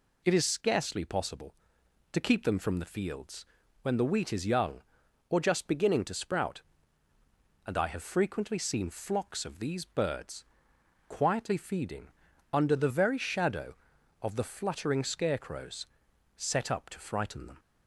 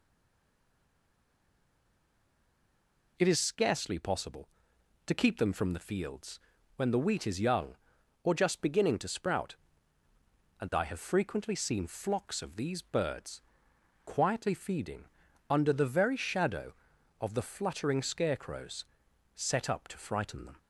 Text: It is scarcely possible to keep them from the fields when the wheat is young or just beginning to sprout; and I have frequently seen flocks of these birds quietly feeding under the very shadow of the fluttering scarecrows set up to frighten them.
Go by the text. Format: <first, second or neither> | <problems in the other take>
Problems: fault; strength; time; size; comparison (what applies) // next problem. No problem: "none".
first | stays silent before the first word; strong; until 3.1 s; 3.1 s long // pauses between "fields" and "when"; at 6.3 s; 0.38 s long; also in the first // pauses between "birds" and "quietly"; noticeable; at 13.4 s; 0.64 s long; noticeable in the first // pauses between "feeding" and "under"; noticeable; at 15.0 s; 0.46 s long; noticeable in the first // pauses between "scarecrows" and "set"; noticeable; at 18.8 s; 0.50 s long; noticeable in the first